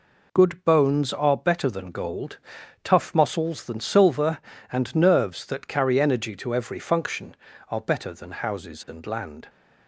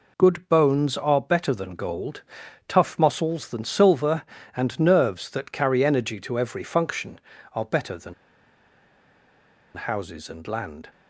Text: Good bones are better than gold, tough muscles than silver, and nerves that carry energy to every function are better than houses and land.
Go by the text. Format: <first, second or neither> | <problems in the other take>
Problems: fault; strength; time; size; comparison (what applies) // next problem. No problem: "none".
first | pauses between "than" and "houses"; strong; at 8.1 s; 1.6 s long